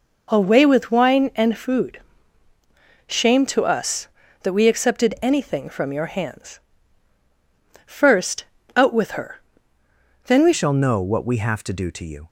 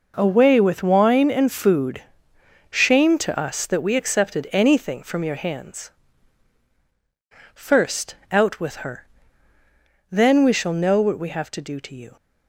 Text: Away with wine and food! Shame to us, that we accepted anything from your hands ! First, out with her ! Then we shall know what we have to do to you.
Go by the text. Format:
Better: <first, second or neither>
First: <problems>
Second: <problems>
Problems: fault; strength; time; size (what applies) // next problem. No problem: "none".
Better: second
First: changes voice at "shall"; from 10.5 s on; 1.7 s long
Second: none